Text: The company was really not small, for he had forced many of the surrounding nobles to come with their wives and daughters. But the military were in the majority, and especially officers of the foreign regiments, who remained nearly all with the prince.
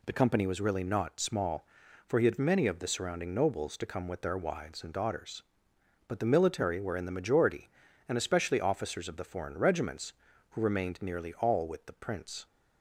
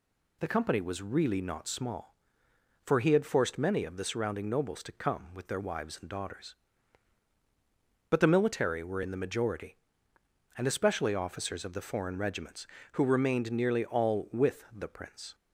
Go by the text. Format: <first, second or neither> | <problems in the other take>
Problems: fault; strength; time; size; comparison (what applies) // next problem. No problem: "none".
second | skips "forced"; at 2.3 s